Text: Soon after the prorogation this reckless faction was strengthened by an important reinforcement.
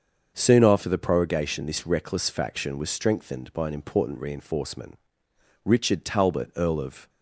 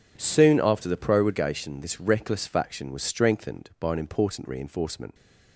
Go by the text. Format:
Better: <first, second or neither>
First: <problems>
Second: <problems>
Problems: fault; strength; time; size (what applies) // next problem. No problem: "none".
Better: second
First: starts louder than the rest; until 1.3 s; 7 dB // goes on to say "Richard Talbot Earl of"; from 5.6 s on; 1.4 s long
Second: none